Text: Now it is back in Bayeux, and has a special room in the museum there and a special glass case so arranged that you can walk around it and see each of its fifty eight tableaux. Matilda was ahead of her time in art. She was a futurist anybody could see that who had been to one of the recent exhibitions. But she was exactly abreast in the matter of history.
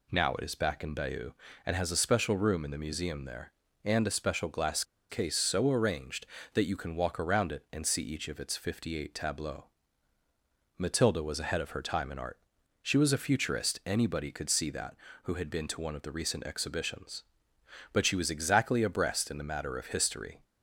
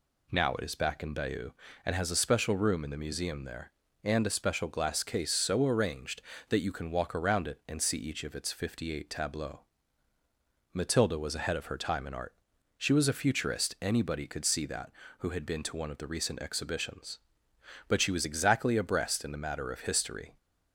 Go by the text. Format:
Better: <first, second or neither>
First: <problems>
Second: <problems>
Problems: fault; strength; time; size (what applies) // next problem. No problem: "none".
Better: second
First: pauses between "glass" and "case"; slight; at 4.8 s; 0.26 s long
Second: none